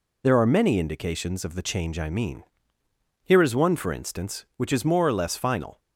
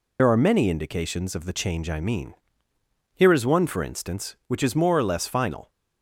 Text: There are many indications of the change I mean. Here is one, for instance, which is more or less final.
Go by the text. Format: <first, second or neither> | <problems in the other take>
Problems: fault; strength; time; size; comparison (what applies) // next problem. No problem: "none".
first | loses the start of "There"; at 0.1 s; 50 ms